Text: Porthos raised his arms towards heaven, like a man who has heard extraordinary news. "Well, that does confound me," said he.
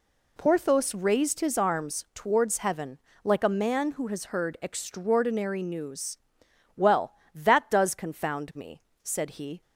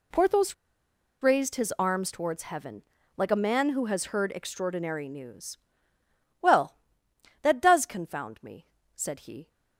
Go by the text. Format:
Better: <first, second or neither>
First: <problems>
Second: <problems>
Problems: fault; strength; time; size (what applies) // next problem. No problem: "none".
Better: first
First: none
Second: pauses between "Porthos" and "raised"; noticeable; at 0.5 s; 0.67 s long